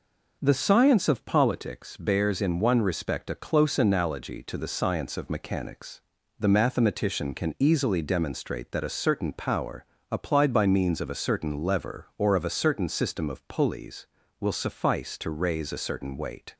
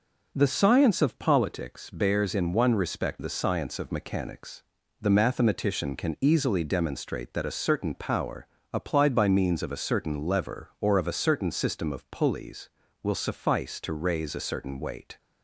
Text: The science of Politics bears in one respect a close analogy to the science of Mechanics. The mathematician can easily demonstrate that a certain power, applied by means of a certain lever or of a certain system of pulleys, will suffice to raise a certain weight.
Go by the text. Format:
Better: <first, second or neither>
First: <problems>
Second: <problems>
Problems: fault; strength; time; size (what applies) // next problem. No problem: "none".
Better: first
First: none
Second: skips "a close analogy to"; at 3.1 s